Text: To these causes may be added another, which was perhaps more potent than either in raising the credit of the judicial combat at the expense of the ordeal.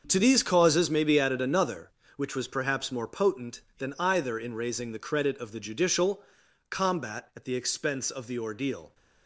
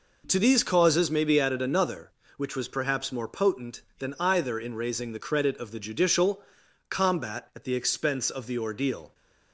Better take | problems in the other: second | gets quieter; strong; throughout; 12 dB // pauses between "judicial" and "combat"; noticeable; at 6.2 s; 0.48 s long; noticeable in the second

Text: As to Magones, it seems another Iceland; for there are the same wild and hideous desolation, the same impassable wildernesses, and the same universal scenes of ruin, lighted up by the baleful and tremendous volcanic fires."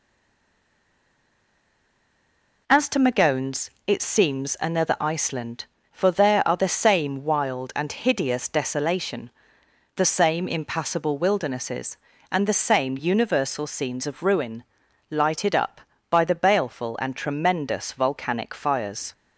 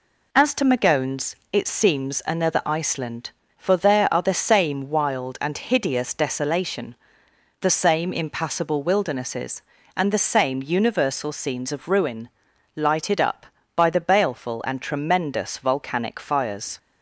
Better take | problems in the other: second | stays silent before the first word; strong; until 2.6 s; 2.6 s long

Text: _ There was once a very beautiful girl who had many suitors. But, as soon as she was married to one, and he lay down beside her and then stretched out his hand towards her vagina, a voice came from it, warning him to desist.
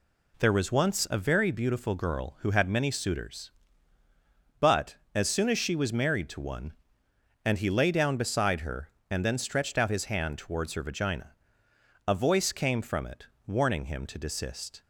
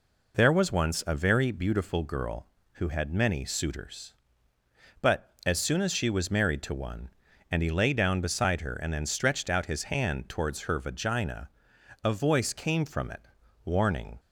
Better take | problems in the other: first | stops before "him to desist"; at 14.1 s

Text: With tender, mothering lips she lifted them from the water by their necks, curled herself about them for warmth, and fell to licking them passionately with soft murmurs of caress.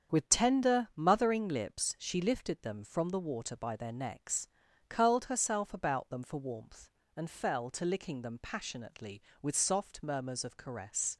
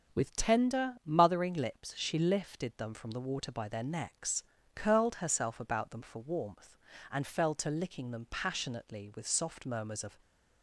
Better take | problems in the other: first | starts louder than the rest; strong; until 1.2 s; 7.5 dB; strong in the first // stops before "caress"; at 10.2 s

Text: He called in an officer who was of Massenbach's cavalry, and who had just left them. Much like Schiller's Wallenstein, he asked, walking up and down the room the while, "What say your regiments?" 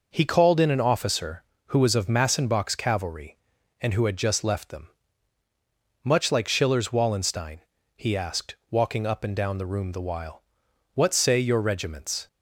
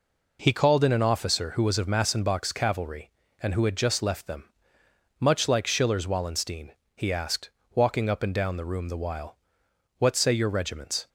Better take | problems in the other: neither | none

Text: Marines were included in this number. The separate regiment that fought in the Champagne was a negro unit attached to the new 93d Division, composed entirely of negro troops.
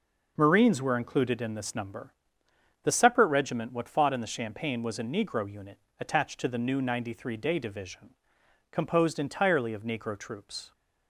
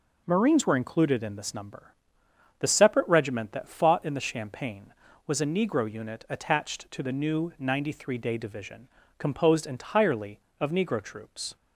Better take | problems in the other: second | says "what" for "that"; at 3.7 s // pauses between "unit" and "attached"; slight; at 5.7 s; 0.20 s long

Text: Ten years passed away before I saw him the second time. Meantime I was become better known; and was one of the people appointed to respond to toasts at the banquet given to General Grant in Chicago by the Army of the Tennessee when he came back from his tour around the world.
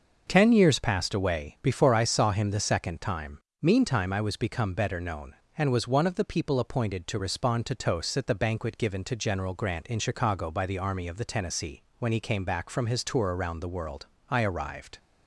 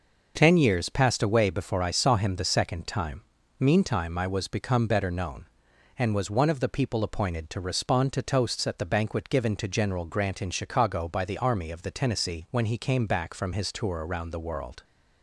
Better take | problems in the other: second | starts louder than the rest; noticeable; until 1.2 s; 6 dB // pauses between "Tennessee" and "when"; slight; at 11.8 s; 0.16 s long // goes on to say "I arrived"; noticeable; from 14.3 s on; 0.66 s long

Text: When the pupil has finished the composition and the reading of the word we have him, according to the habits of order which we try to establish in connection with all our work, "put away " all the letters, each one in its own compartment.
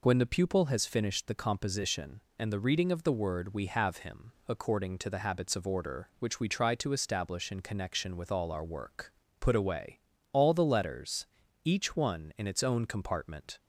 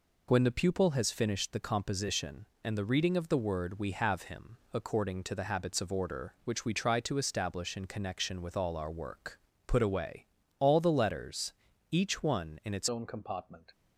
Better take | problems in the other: first | changes voice at "own"; from 12.8 s on; 0.9 s long

